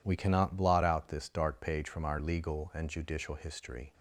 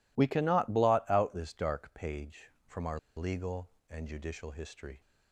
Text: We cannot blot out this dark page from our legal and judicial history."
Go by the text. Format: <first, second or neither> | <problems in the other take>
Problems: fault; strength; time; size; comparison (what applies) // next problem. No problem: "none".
first | pauses between "our" and "legal"; slight; at 2.9 s; 0.17 s long